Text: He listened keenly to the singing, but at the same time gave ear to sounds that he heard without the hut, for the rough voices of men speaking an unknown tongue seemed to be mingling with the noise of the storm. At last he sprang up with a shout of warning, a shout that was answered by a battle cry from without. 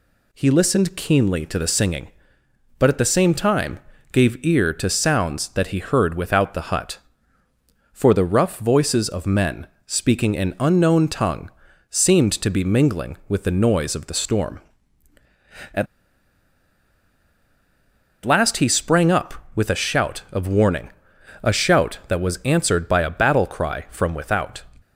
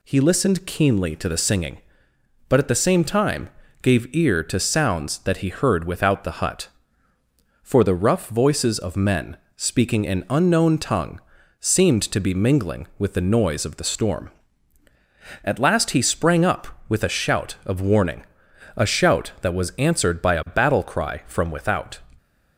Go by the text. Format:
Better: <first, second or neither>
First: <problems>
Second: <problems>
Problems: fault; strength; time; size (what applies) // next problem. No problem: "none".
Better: second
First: pauses between "time" and "gave"; slight; at 3.7 s; 0.32 s long // pauses between "men" and "speaking"; slight; at 9.6 s; 0.18 s long // pauses between "tongue" and "seemed"; at 11.4 s; 0.40 s long // pauses between "At" and "last"; strong; at 15.8 s; 2.3 s long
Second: pauses between "time" and "gave"; slight; at 3.4 s; 0.32 s long // pauses between "men" and "speaking"; slight; at 9.3 s; 0.18 s long // pauses between "tongue" and "seemed"; at 11.1 s; 0.40 s long